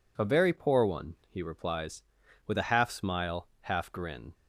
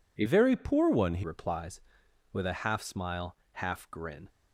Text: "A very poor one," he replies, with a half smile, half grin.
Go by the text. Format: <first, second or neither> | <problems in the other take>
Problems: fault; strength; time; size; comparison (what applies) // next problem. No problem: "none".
first | changes voice from "very" to "he"; from 0.2 to 1.2 s; 1.0 s long